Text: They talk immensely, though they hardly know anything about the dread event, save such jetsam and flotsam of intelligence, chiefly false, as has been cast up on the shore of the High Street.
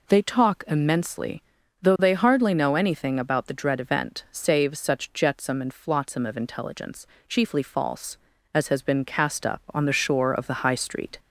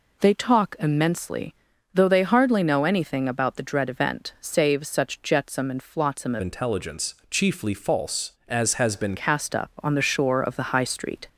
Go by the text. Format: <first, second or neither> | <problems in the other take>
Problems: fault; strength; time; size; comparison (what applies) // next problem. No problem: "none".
first | changes voice from "intelligence" to "been"; from 6.4 to 9.1 s; 2.7 s long